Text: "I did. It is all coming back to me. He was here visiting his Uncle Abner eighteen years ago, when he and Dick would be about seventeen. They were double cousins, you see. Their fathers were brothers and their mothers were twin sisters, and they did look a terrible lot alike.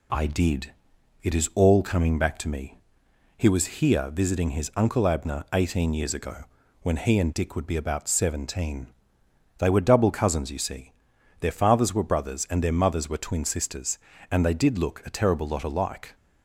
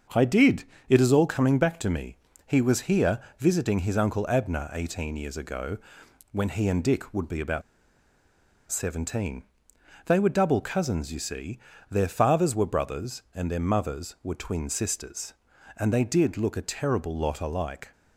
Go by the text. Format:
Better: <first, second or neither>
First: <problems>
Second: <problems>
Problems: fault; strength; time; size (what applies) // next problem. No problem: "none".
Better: first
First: none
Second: starts louder than the rest; until 1.3 s; 6.5 dB // pauses between "here" and "visiting"; slight; at 3.2 s; 0.16 s long // pauses between "about" and "seventeen"; at 7.6 s; 1.0 s long